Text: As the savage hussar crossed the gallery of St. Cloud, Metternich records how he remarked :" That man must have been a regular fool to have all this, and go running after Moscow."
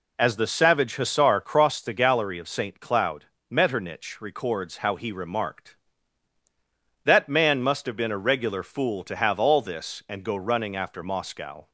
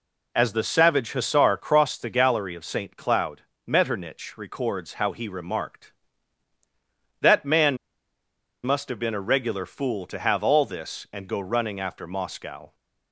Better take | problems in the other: first | pauses between "man" and "must"; noticeable; at 7.7 s; 0.88 s long

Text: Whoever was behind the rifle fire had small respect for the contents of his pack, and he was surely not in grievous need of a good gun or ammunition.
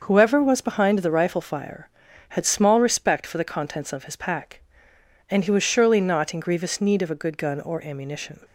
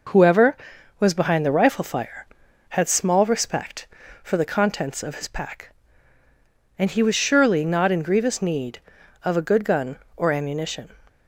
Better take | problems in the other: neither | none

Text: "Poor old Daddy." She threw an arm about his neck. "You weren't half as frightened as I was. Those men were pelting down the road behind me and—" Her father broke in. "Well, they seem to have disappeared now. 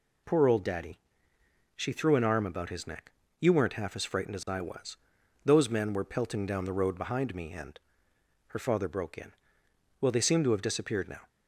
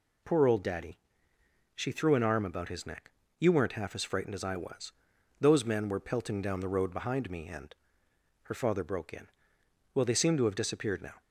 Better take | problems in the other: neither | none

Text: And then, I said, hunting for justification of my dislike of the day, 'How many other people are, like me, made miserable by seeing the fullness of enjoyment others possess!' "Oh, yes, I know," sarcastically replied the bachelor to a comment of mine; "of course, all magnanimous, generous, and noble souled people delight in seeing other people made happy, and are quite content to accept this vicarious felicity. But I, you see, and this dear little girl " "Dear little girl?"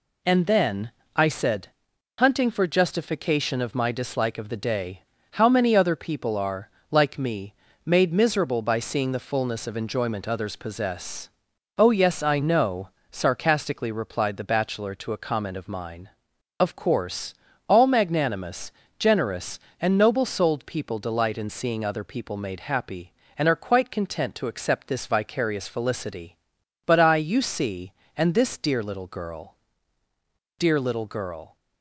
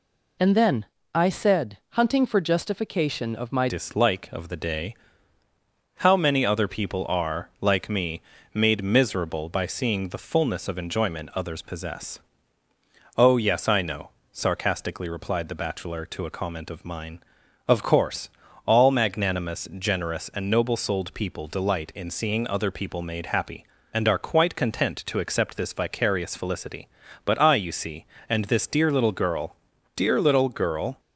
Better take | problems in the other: first | changes voice at "dislike"; from 3.6 s on; 27.3 s long

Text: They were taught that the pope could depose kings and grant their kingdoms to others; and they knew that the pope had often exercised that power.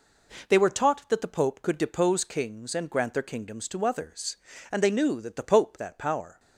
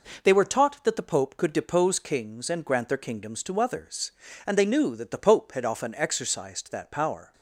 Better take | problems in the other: second | skips "had often exercised"; at 5.7 s

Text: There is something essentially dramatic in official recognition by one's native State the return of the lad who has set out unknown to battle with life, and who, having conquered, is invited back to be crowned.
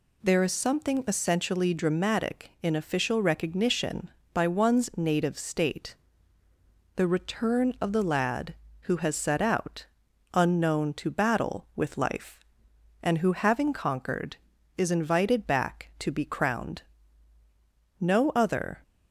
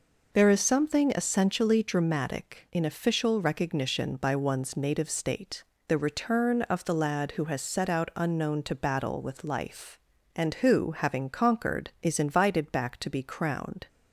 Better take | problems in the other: second | pauses between "State" and "the"; at 5.9 s; 1.0 s long; slight in the second // pauses between "out" and "unknown"; noticeable; at 9.8 s; 0.48 s long // goes on to say "No other"; noticeable; from 17.9 s on; 0.84 s long

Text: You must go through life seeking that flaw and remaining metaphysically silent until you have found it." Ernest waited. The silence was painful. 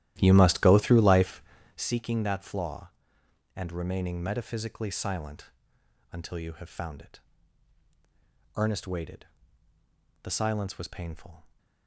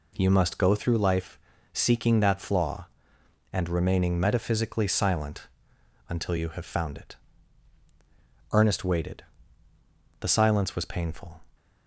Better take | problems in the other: second | starts louder than the rest; strong; until 1.8 s; 13 dB // pauses between "life" and "seeking"; at 1.4 s; 0.38 s long; also in the second // pauses between "silent" and "until"; noticeable; at 5.5 s; 0.60 s long; noticeable in the second

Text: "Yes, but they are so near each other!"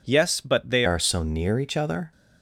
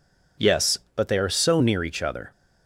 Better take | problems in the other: second | changes voice at "are"; from 0.8 s on; 1.3 s long

